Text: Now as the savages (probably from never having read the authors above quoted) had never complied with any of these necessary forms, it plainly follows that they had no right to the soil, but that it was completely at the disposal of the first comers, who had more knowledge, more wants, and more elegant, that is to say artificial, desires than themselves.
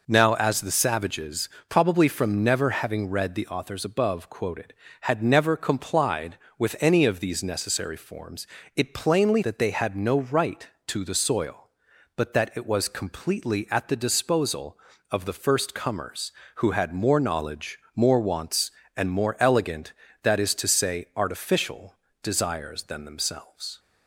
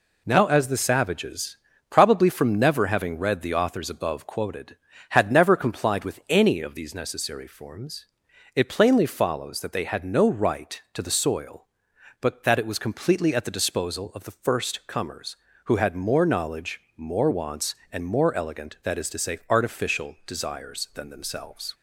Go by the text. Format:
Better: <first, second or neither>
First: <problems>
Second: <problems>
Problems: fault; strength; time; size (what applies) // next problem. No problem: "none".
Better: second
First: skips "follows"; at 9.4 s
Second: none